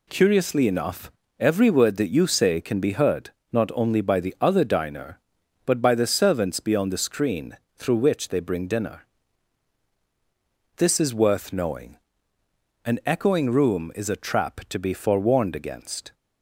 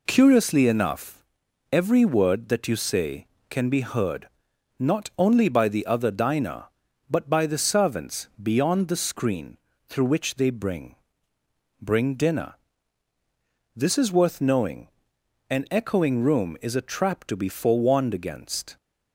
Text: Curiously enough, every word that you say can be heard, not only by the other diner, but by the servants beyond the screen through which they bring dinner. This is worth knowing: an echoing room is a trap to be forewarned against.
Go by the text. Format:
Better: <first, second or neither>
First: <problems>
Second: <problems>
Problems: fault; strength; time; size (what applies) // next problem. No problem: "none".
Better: first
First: pauses between "screen" and "through"; slight; at 7.5 s; 0.18 s long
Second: pauses between "screen" and "through"; slight; at 9.5 s; 0.30 s long // says "bring" twice; at 11.8 s